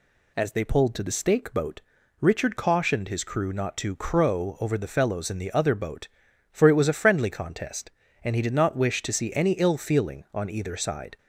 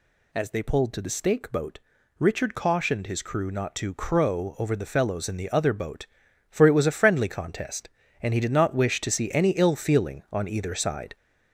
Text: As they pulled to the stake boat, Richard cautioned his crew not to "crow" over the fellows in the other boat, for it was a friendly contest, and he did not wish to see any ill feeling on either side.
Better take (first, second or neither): first